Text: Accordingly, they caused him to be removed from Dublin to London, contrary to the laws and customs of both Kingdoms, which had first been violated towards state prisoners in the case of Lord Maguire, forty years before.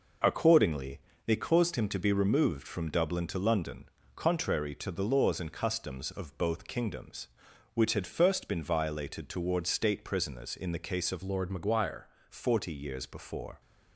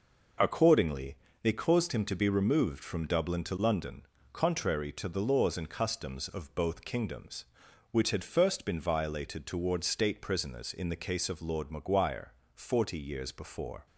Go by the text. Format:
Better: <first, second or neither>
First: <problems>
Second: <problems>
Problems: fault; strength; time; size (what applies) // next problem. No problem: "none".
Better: second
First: changes voice from "Lord" to "Maguire"; from 11.2 to 12.0 s; 0.8 s long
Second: none